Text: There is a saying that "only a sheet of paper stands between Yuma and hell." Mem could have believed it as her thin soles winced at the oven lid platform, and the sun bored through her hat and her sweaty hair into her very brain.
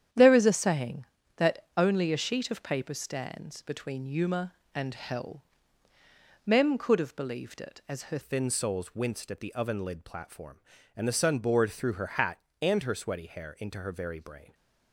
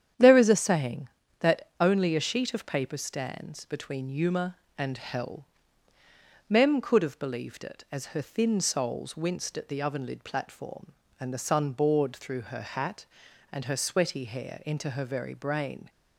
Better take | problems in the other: second | starts louder than the rest; strong; until 1.4 s; 9.5 dB; strong in the second // changes voice at "thin"; from 8.2 s on; 6.3 s long

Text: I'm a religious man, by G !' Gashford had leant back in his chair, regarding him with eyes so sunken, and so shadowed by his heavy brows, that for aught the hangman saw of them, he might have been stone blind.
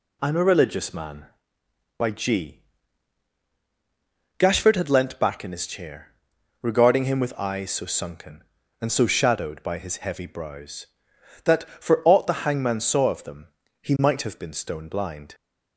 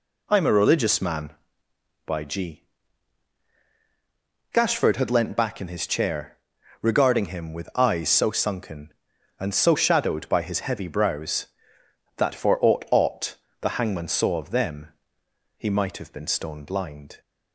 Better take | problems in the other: first | says "aught" twice; at 12.9 s

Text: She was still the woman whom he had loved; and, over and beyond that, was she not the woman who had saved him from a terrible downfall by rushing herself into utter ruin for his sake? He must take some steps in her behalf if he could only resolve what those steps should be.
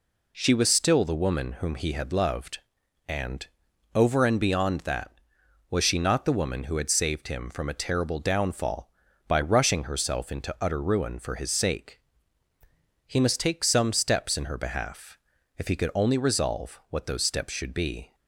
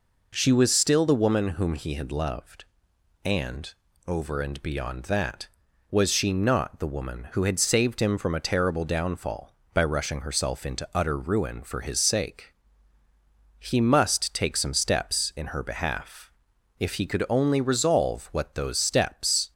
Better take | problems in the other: first | pauses between "behalf" and "if"; noticeable; at 16.3 s; 0.46 s long; also in the first // stops before "should be"; at 19.5 s

